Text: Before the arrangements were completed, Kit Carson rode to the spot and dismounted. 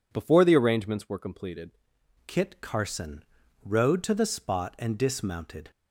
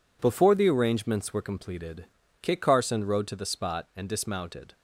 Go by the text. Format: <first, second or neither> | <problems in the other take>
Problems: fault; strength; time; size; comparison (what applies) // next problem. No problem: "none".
second | changes voice at "Kit"; from 2.2 s on; 3.5 s long // pauses between "Carson" and "rode"; at 3.2 s; 0.40 s long